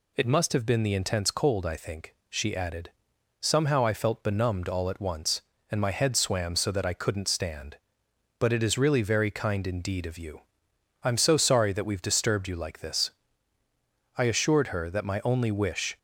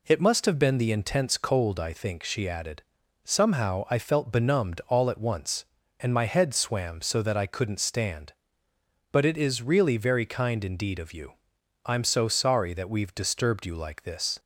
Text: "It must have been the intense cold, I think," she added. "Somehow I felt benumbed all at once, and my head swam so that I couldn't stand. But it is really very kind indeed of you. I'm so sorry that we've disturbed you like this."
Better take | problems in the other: second | goes on to say "I assured her that my only wish"; strong; from 14.1 s on; 1.8 s long

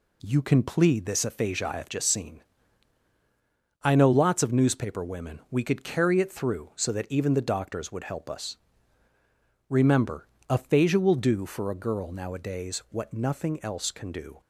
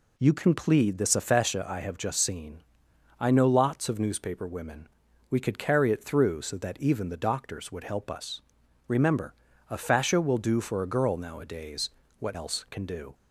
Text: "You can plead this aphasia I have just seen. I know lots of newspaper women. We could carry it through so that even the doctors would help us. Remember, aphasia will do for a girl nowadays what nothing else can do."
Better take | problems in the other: first | pauses between "nowadays" and "what"; slight; at 11.9 s; 0.30 s long // skips "nothing"; at 12.3 s

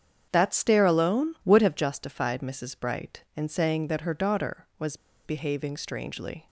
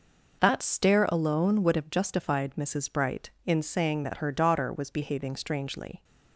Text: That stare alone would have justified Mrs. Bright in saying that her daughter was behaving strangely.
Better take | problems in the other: second | starts louder than the rest; strong; until 1.3 s; 8 dB // pauses between "was" and "behaving"; slight; at 4.9 s; 0.28 s long

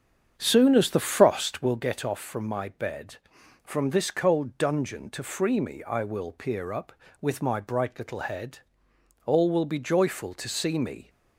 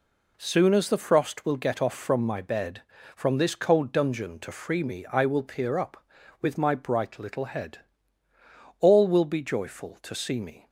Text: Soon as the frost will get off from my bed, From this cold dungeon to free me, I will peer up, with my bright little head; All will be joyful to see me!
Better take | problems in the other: second | starts louder than the rest; strong; until 1.7 s; 8 dB

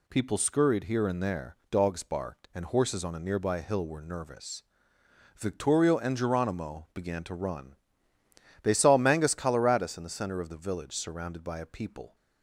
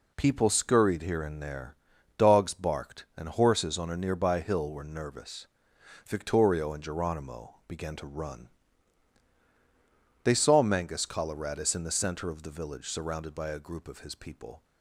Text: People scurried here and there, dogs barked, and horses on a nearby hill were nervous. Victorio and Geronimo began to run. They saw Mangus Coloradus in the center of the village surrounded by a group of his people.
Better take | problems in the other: second | skips "group of his"; at 11.6 s

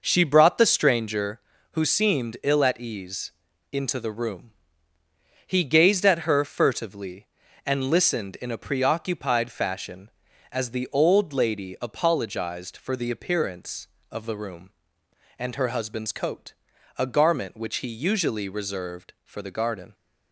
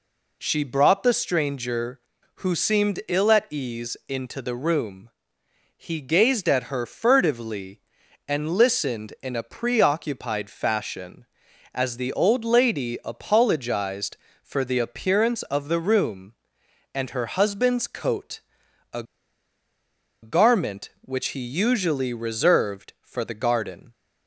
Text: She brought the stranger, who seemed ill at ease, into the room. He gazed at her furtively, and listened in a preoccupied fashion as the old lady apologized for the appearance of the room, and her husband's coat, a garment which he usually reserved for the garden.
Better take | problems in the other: first | pauses between "a" and "garment"; at 19.0 s; 1.1 s long

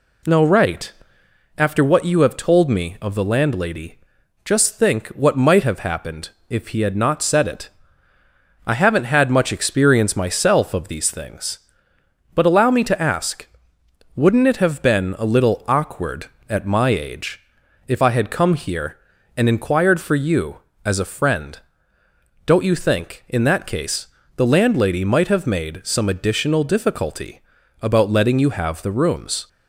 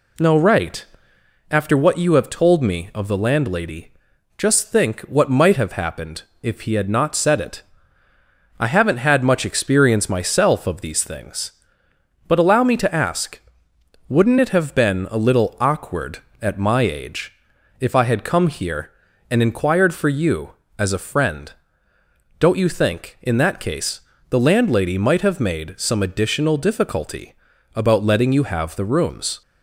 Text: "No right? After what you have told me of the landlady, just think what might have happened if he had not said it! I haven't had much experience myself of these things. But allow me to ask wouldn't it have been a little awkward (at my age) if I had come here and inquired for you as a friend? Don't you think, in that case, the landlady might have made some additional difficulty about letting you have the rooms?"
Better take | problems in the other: neither | pauses between "happened" and "if"; slight; the same in both // pauses between "ask" and "wouldn't"; noticeable; the same in both // pauses between "difficulty" and "about"; the same in both

